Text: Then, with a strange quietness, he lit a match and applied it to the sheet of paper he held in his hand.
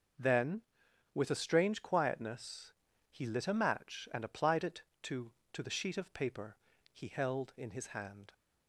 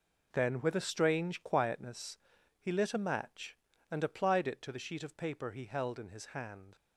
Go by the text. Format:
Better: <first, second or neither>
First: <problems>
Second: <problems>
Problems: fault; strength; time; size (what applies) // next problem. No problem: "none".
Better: second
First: starts louder than the rest; until 1.7 s; 6 dB // says "to" twice; at 5.5 s // pauses between "paper" and "he"; slight; at 6.5 s; 0.36 s long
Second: none